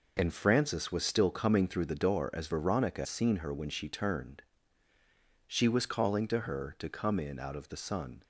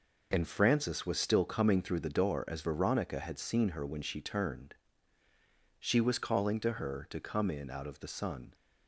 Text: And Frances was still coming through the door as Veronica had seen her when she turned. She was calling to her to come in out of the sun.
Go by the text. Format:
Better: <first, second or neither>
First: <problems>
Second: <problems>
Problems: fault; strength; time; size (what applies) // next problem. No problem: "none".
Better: second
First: skips "had"; at 3.0 s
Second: none